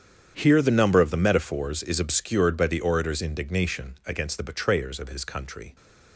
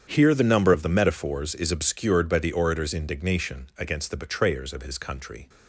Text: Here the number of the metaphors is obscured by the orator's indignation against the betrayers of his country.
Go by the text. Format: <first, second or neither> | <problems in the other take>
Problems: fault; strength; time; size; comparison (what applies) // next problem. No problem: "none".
neither | starts louder than the rest; strong; the same in both